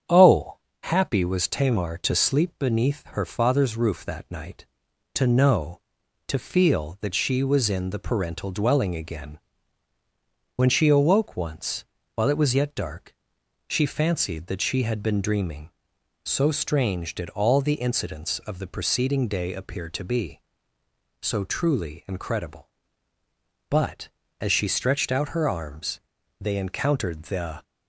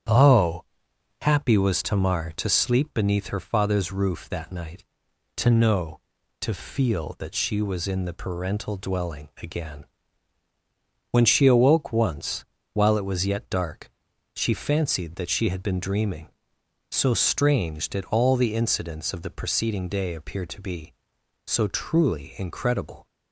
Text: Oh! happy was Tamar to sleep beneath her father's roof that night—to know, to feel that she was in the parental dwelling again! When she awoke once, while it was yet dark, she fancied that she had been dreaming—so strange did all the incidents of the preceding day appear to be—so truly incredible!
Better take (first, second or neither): second